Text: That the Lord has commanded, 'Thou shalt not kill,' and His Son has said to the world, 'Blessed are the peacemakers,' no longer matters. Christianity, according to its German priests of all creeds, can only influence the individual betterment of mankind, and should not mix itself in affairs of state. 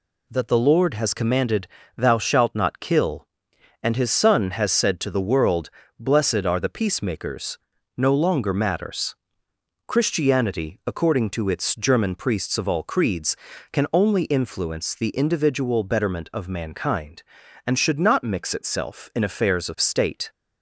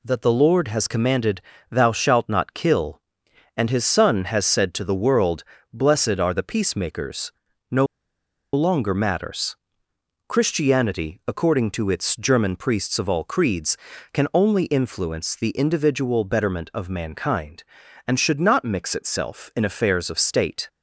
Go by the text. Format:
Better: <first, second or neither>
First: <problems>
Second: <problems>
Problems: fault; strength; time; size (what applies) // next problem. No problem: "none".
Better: first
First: none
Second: pauses between "no" and "longer"; noticeable; at 7.8 s; 0.67 s long